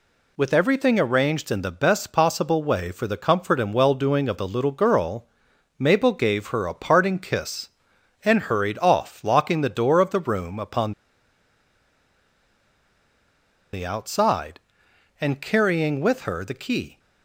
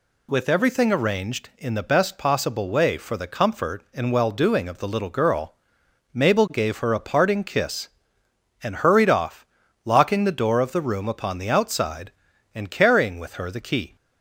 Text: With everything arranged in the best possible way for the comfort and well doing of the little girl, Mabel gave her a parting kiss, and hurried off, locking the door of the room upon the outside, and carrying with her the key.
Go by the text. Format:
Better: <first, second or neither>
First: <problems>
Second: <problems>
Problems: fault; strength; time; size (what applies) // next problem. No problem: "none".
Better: second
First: pauses between "upon" and "the"; strong; at 10.9 s; 2.7 s long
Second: none